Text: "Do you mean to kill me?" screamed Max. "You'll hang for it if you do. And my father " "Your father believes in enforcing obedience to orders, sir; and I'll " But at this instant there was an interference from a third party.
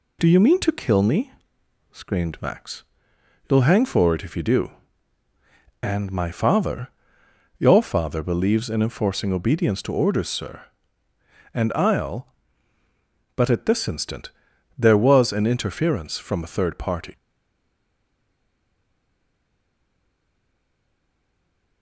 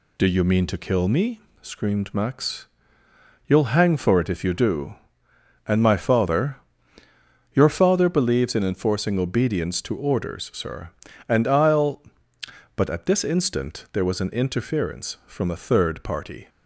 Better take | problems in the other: second | pauses between "instant" and "there"; noticeable; at 14.2 s; 0.48 s long // stays silent after the last word; strong; from 17.1 s on; 4.7 s long

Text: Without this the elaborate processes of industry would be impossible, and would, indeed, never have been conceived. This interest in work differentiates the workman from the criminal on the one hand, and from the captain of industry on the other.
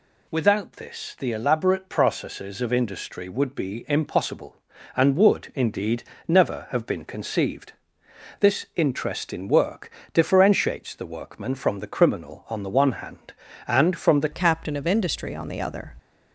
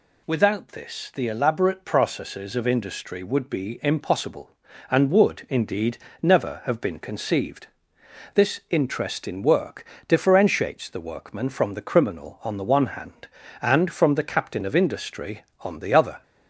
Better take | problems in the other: second | pauses between "work" and "differentiates"; slight; at 9.8 s; 0.22 s long; slight in the second // changes voice at "captain"; from 14.3 s on; 1.6 s long

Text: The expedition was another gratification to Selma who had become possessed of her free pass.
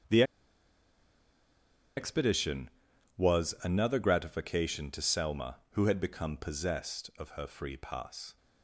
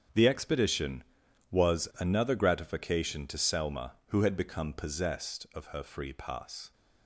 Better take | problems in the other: second | starts louder than the rest; strong; until 3.3 s; 8 dB; strong in the second // pauses between "The" and "expedition"; strong; at 0.2 s; 1.7 s long

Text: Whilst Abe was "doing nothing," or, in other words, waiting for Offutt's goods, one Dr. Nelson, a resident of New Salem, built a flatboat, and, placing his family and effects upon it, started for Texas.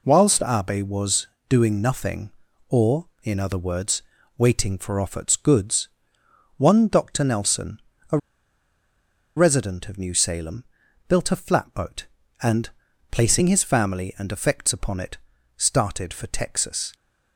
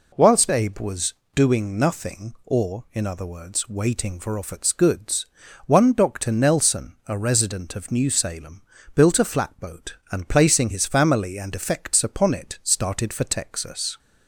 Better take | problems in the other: second | pauses between "was" and "doing"; slight; at 1.2 s; 0.20 s long; slight in the second // pauses between "a" and "resident"; at 8.1 s; 1.1 s long

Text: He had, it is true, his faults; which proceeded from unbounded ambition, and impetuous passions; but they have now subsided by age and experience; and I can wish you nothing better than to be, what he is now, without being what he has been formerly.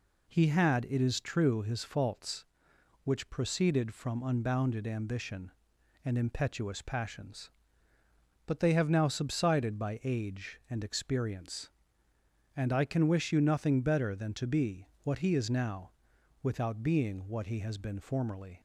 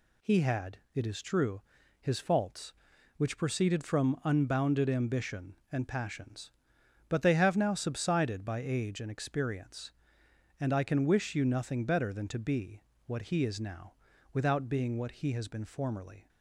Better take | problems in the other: first | skips "impetuous"; at 5.8 s

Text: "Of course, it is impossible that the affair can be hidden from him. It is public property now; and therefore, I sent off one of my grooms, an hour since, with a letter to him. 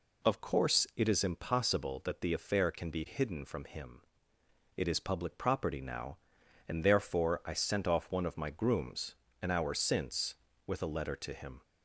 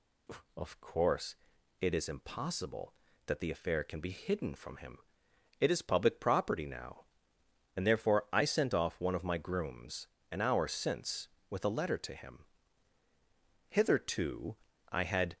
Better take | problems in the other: first | goes on to say "Hitherto I had"; strong; from 13.6 s on; 1.6 s long

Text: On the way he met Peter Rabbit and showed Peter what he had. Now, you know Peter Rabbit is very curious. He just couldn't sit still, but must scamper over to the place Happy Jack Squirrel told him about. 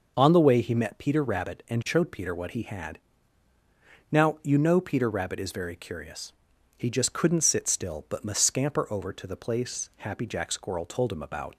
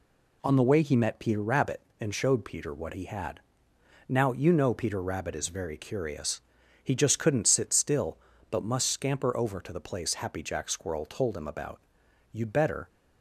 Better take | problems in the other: first | goes on to say "You'd better"; from 12.3 s on; 0.56 s long

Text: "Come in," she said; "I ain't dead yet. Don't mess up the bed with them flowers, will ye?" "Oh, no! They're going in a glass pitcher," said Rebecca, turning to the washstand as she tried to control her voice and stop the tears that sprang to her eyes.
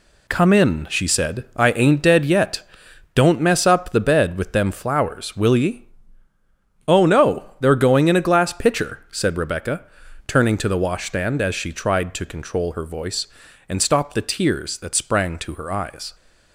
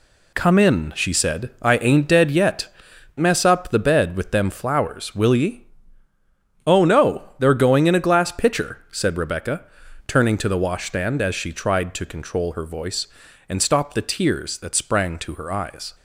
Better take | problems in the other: first | skips "Don't"; at 2.9 s

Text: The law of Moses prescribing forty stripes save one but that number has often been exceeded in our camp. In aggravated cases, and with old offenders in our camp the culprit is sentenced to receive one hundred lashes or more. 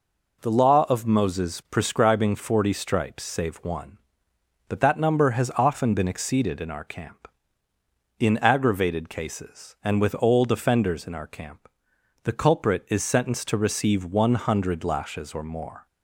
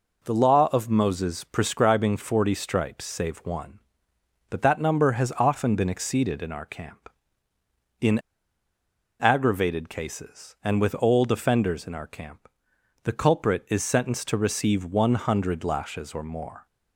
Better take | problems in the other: first | pauses between "In" and "aggravated"; at 8.1 s; 1.0 s long // pauses between "camp" and "the"; noticeable; at 12.4 s; 0.54 s long; noticeable in the first

